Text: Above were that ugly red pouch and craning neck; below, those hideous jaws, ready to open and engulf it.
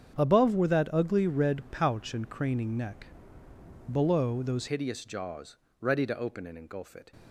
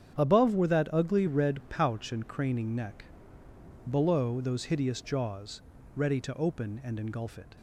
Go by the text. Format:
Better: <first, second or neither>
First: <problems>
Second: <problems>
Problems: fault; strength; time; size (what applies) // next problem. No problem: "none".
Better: second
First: starts louder than the rest; strong; until 1.2 s; 9 dB // changes voice at "hideous"; from 4.6 s on; 2.5 s long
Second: starts louder than the rest; strong; until 1.2 s; 10 dB